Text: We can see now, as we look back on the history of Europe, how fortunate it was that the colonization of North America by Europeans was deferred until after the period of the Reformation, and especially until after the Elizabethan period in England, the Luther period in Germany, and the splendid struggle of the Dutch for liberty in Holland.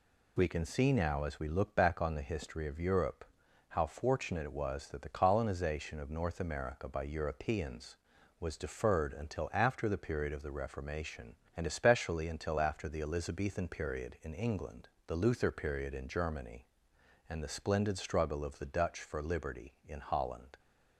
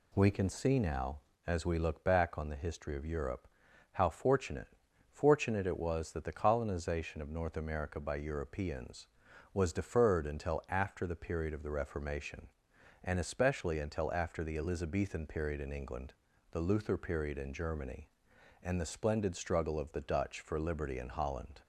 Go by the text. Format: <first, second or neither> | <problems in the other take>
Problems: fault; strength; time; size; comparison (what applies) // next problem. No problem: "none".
first | says "fortunate" twice; at 5.0 s